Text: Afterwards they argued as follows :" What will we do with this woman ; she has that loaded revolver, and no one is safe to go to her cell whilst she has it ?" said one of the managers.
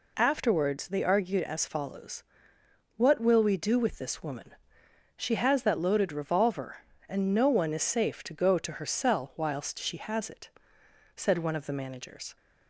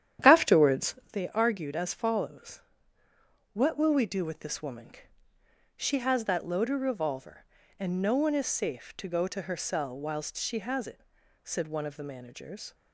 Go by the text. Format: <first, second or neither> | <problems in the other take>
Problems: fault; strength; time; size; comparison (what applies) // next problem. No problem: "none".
first | starts louder than the rest; strong; until 1.2 s; 10 dB // pauses between "Afterwards" and "they"; slight; at 0.9 s; 0.16 s long